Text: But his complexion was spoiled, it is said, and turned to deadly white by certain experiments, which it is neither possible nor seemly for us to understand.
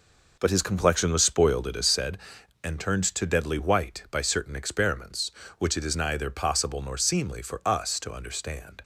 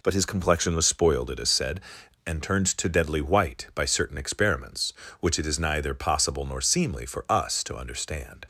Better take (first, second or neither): second